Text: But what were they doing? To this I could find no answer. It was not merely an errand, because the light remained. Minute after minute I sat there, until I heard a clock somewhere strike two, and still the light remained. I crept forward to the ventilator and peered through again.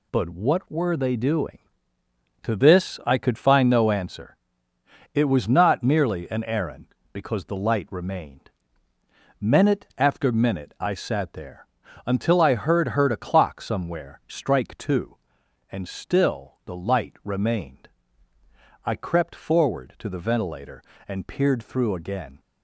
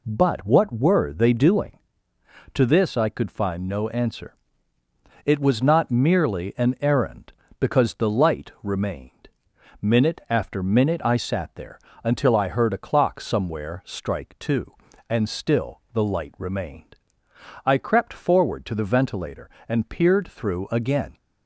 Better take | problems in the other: second | says "heard" twice; at 12.8 s

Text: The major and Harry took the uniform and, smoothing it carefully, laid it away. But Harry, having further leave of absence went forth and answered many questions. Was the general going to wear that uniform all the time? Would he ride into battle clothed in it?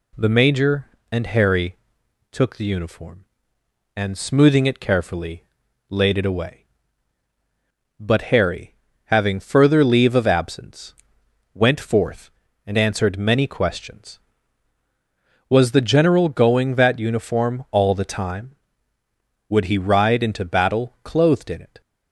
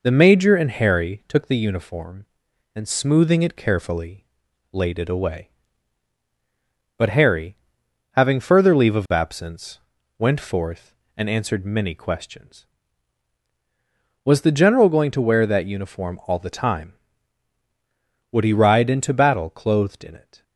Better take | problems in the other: second | pauses between "Harry" and "took"; noticeable; at 1.7 s; 0.54 s long // pauses between "absence" and "went"; noticeable; at 10.9 s; 0.62 s long; also in the second // skips "to wear"; at 16.7 s

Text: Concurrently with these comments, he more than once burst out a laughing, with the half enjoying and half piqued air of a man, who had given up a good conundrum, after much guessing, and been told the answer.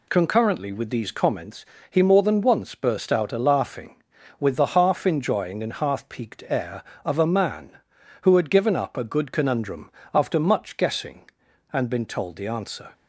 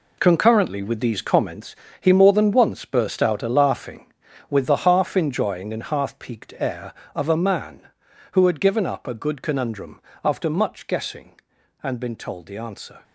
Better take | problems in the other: first | gets quieter; strong; throughout; 11 dB

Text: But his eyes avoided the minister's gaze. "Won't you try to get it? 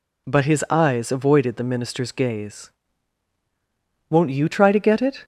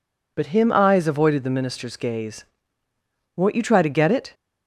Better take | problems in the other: first | says "him" for "his"; at 0.4 s

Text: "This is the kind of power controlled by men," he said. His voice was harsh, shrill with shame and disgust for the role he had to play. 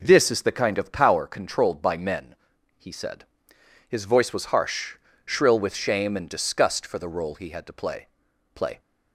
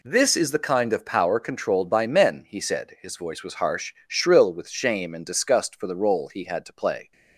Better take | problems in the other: second | says "play" twice; at 8.5 s

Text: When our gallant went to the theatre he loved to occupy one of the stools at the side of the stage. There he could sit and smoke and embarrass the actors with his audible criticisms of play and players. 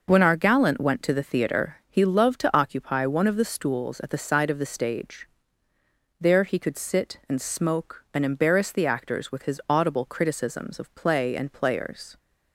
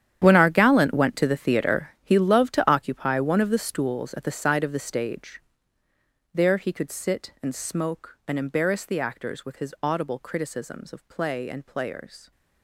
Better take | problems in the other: first | gets quieter; strong; throughout; 14.5 dB

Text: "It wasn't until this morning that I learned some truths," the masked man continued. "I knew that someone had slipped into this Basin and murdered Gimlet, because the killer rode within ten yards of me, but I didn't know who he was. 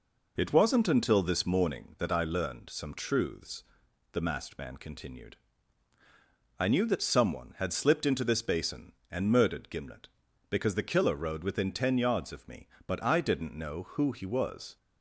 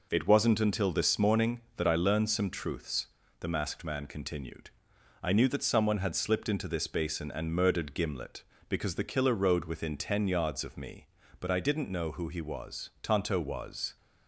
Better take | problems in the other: first | goes on to say "Tonto was"; noticeable; from 13.0 s on; 0.92 s long

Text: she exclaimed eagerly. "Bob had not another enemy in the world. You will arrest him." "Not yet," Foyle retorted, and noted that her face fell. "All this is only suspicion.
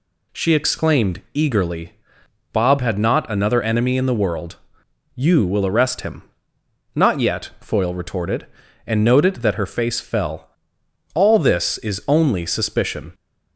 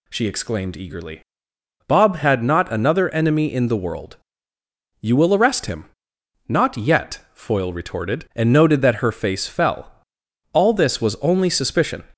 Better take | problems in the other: first | says "was" for "is"; at 11.0 s

